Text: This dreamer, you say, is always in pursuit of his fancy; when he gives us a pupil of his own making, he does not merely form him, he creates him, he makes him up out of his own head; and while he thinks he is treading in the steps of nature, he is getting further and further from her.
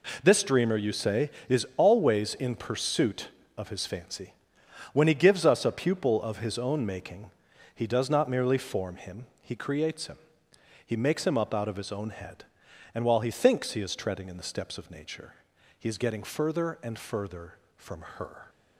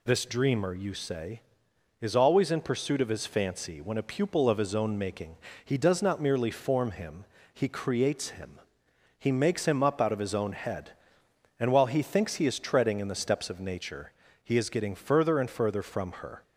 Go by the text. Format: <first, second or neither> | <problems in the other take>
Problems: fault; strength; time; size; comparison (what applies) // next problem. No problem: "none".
first | skips "he gives us"; at 3.9 s